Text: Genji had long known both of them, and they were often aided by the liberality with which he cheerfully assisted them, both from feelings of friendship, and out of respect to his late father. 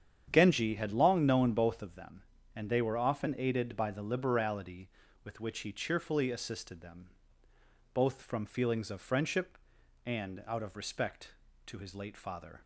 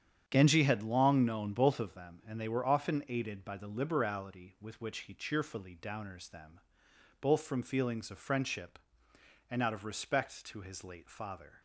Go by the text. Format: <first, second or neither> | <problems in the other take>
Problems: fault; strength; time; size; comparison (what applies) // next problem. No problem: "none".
first | starts louder than the rest; strong; until 1.2 s; 8.5 dB; strong in the first // says "downers" for "assisted"; at 5.8 s